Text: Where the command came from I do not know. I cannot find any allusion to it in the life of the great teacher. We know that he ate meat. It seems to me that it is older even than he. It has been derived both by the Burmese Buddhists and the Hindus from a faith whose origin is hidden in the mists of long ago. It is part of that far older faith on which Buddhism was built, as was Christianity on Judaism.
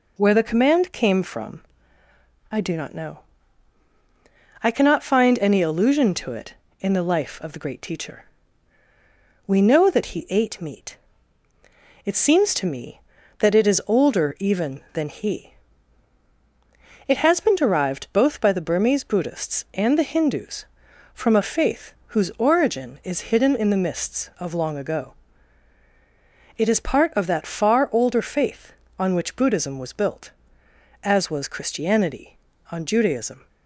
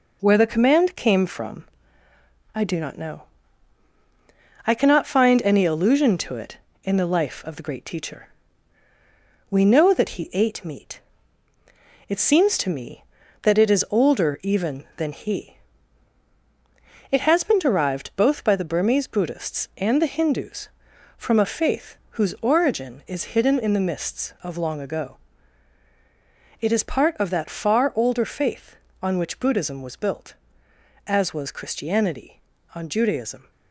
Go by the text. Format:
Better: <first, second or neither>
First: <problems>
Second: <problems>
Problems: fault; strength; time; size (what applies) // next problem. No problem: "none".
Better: first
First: pauses between "from" and "I"; noticeable; at 1.6 s; 0.90 s long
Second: gets quieter; noticeable; throughout; 5 dB // pauses between "from" and "I"; noticeable; at 1.6 s; 0.90 s long